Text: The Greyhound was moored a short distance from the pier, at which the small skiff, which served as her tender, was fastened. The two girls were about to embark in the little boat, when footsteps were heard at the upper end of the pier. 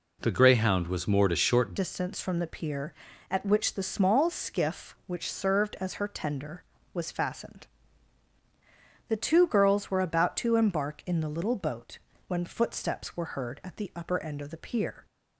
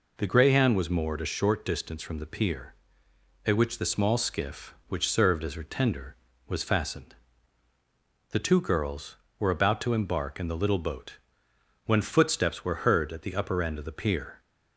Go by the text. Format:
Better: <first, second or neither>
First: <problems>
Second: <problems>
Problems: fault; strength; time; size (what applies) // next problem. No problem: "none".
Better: second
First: changes voice at "distance"; from 1.7 s on; 13.3 s long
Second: none